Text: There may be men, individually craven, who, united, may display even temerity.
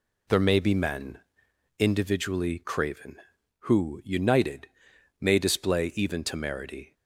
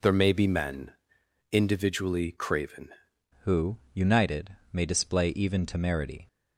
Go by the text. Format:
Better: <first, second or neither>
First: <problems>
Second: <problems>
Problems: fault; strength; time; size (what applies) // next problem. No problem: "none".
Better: first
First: none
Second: changes voice at "who"; from 3.4 s on; 2.8 s long